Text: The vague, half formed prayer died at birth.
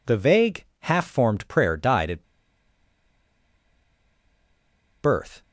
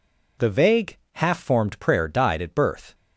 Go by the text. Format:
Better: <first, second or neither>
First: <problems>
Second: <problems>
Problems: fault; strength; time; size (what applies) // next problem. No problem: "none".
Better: second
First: pauses between "at" and "birth"; strong; at 2.2 s; 2.8 s long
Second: none